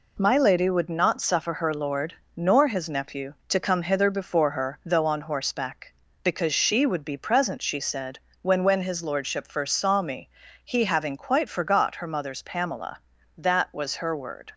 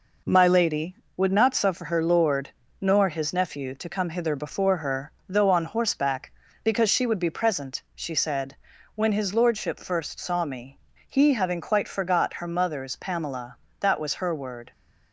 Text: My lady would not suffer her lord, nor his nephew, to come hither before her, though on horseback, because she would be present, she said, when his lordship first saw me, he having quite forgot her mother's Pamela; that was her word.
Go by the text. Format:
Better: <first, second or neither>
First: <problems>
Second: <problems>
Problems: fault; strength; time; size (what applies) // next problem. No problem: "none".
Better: second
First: says "when" twice; at 8.6 s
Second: none